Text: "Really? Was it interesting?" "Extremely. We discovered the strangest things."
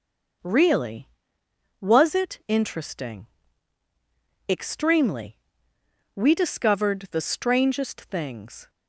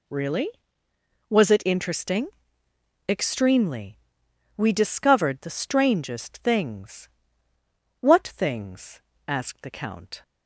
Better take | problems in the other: first | goes on to say "What things asked the count"; strong; from 7.9 s on; 2.2 s long

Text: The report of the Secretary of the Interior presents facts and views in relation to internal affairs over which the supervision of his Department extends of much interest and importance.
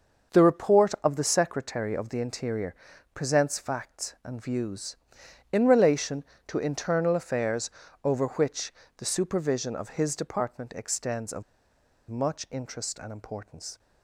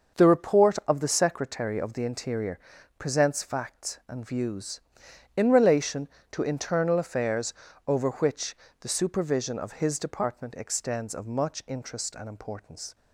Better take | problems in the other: second | starts louder than the rest; until 1.4 s; 6.5 dB; also in the second // pauses between "Interior" and "presents"; at 2.7 s; 0.40 s long; also in the second // pauses between "affairs" and "over"; slight; at 7.7 s; 0.32 s long; slight in the second // pauses between "which" and "the"; slight; at 8.7 s; 0.26 s long; slight in the second // pauses between "of" and "much"; noticeable; at 11.4 s; 0.67 s long

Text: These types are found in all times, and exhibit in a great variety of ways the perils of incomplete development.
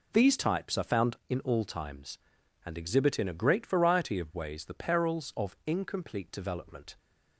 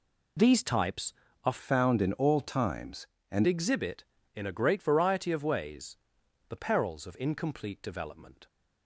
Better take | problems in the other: first | changes voice from "found" to "and"; from 1.6 to 3.4 s; 1.8 s long // pauses between "ways" and "the"; noticeable; at 5.9 s; 0.52 s long

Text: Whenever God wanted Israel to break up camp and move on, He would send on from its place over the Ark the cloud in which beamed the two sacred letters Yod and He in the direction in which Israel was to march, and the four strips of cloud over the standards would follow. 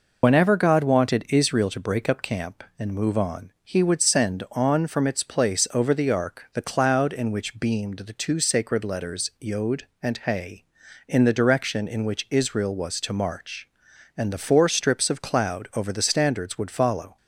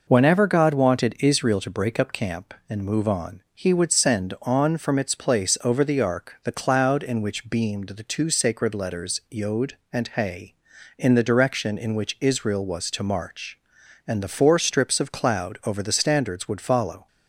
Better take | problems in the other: second | loses the start of "Whenever"; at 0.2 s; 55 ms

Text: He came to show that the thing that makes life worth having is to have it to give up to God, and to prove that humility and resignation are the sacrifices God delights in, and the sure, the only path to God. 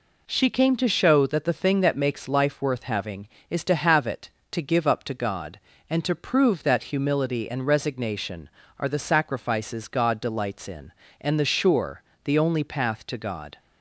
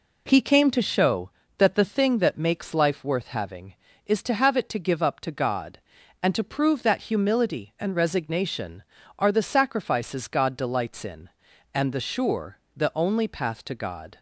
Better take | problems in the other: second | says "She" for "He"; at 0.2 s

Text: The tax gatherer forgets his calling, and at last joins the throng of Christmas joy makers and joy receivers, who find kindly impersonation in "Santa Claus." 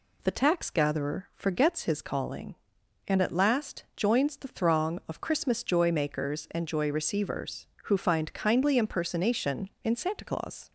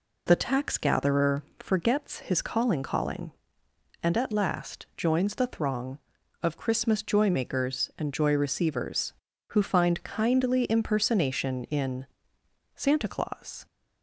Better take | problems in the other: first | pauses between "gatherer" and "forgets"; slight; at 1.4 s; 0.16 s long // says "calling" twice; at 2.8 s // pauses between "in" and "Santa"; noticeable; at 12.0 s; 0.69 s long

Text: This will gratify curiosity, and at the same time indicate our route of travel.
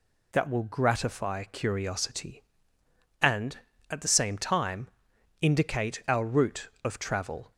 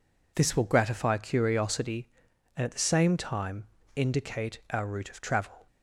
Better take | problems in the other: second | says "That" for "This"; at 0.3 s // pauses between "time" and "indicate"; noticeable; at 4.8 s; 0.52 s long; slight in the second

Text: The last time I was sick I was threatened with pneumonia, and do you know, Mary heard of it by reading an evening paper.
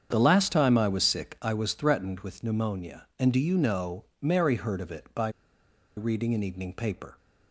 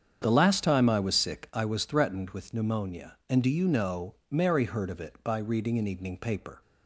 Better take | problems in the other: second | starts louder than the rest; strong; until 1.1 s; 7.5 dB; strong in the second // pauses between "by" and "reading"; noticeable; at 5.2 s; 0.67 s long

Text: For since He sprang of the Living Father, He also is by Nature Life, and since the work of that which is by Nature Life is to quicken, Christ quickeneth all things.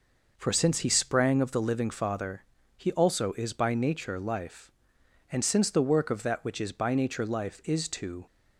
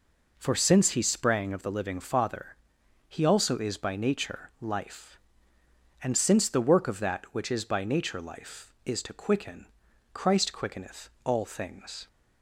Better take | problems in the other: second | stops before "quicken Christ quickeneth all things"; at 8.2 s

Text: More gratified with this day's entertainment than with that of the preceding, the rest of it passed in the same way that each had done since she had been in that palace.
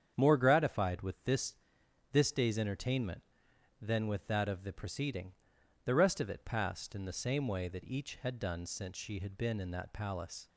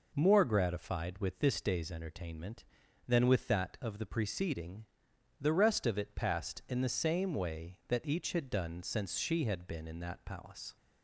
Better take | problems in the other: second | starts louder than the rest; strong; until 1.1 s; 8 dB // says "this" twice; at 2.1 s

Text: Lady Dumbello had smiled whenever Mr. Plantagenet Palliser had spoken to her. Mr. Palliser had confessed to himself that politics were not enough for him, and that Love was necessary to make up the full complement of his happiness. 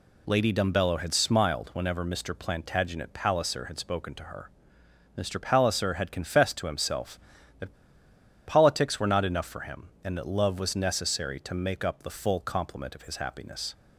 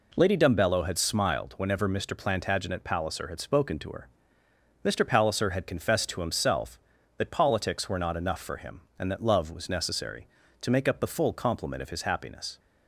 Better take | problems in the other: second | pauses between "that" and "politics"; noticeable; at 7.7 s; 0.74 s long

